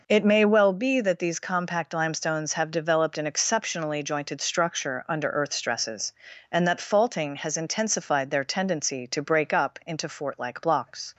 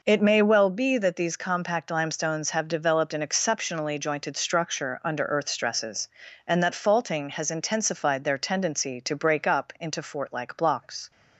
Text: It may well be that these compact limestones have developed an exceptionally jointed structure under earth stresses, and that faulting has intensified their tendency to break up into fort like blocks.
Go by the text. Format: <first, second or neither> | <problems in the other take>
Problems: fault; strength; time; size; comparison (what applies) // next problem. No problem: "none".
neither | none